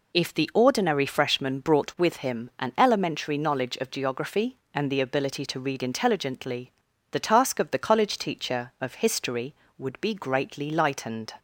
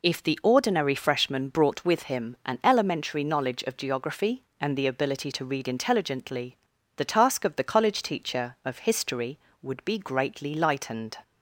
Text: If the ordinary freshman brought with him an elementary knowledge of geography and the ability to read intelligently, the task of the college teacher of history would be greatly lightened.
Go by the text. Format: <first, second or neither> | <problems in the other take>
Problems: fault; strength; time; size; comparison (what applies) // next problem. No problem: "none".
neither | none